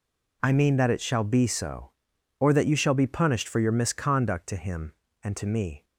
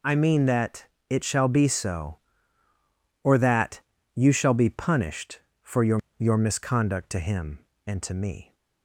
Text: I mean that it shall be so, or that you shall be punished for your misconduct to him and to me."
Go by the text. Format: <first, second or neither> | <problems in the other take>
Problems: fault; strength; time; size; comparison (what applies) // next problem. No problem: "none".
first | pauses between "that" and "it"; slight; at 0.8 s; 0.24 s long // pauses between "that" and "you"; slight; at 3.7 s; 0.34 s long // says "your" twice; at 6.1 s